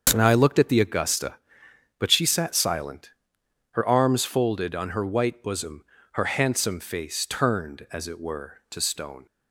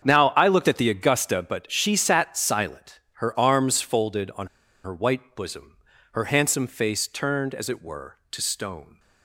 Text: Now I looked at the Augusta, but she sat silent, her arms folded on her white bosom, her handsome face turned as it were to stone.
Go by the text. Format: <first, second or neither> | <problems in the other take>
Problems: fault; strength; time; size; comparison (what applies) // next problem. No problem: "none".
first | starts louder than the rest; strong; until 1.0 s; 7.5 dB; also in the first // pauses between "on" and "her"; at 4.4 s; 0.37 s long